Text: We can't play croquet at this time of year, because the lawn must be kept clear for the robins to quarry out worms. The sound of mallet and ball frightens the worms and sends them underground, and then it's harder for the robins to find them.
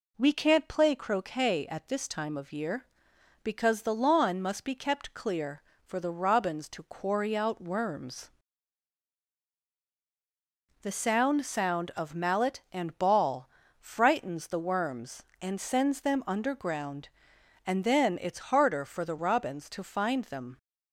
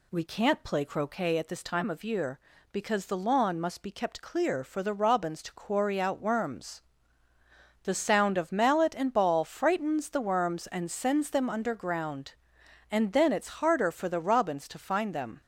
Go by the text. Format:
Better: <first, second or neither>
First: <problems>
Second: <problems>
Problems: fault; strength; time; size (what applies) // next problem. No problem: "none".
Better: second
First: says "sound" twice; at 11.4 s // pauses between "ball" and "frightens"; slight; at 13.4 s; 0.32 s long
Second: none